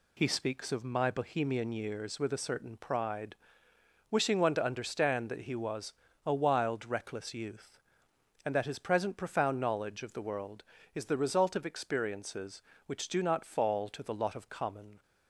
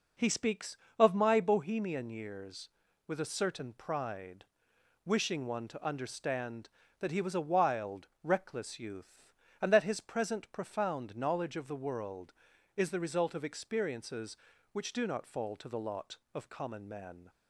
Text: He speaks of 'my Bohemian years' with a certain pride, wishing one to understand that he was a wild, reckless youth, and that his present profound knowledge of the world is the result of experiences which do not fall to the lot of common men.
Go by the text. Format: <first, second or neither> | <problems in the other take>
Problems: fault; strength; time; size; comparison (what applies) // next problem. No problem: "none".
second | pauses between "was" and "a"; slight; at 5.9 s; 0.34 s long // stops before "men"; at 15.0 s